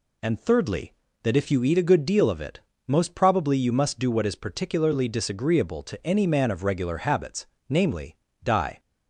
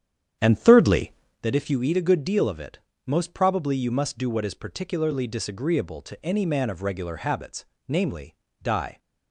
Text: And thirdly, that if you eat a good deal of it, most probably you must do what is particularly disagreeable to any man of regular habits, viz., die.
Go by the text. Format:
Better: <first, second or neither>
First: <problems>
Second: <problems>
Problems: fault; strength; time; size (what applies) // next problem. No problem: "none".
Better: first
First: none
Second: starts louder than the rest; strong; until 1.4 s; 9 dB